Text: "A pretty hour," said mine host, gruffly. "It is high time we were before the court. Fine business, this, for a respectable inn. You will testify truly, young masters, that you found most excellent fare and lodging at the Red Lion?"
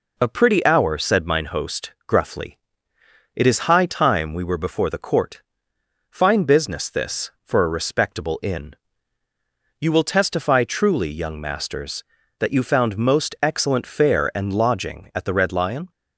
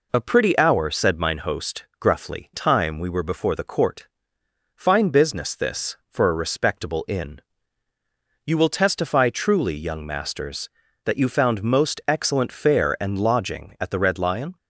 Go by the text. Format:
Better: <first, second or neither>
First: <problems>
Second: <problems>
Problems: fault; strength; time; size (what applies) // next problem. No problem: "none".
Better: first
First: none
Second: skips "It is high"; at 2.5 s